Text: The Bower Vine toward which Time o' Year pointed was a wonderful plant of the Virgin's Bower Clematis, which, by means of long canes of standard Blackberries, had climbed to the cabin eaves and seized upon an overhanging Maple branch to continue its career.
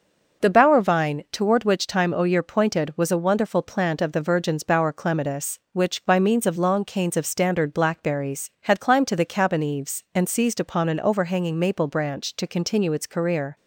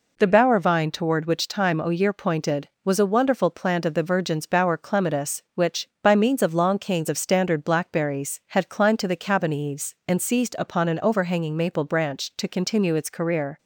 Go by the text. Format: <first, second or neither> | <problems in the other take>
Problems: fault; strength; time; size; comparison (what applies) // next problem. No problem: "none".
neither | none